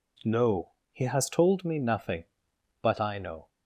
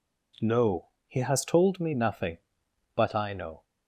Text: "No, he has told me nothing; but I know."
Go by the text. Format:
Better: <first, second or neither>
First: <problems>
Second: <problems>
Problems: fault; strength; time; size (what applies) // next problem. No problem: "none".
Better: neither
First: none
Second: none